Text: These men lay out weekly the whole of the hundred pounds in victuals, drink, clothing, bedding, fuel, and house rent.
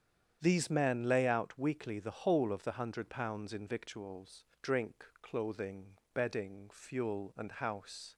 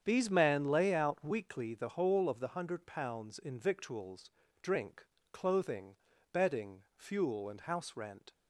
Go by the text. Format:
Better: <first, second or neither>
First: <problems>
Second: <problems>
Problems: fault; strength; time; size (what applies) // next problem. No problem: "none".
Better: second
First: starts louder than the rest; strong; until 1.4 s; 8.5 dB // stops before "rent"; at 8.1 s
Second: starts louder than the rest; strong; until 1.0 s; 8 dB